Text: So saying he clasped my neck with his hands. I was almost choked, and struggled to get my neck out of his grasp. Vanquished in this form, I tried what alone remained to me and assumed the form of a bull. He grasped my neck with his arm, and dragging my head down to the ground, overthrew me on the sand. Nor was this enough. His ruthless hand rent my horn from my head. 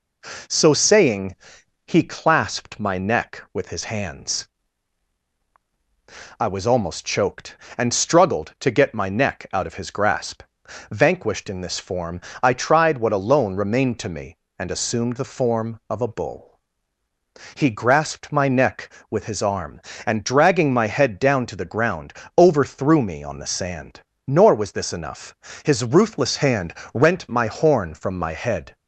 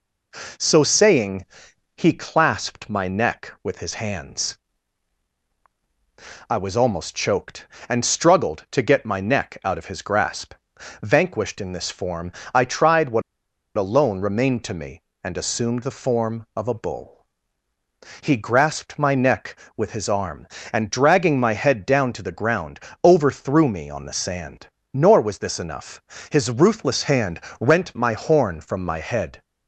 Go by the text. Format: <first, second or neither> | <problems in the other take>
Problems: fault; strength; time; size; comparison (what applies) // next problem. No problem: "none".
first | pauses between "saying" and "he"; noticeable; at 1.4 s; 0.54 s long; noticeable in the first // pauses between "what" and "alone"; noticeable; at 13.2 s; 0.55 s long // pauses between "hand" and "rent"; slight; at 27.3 s; 0.22 s long; slight in the first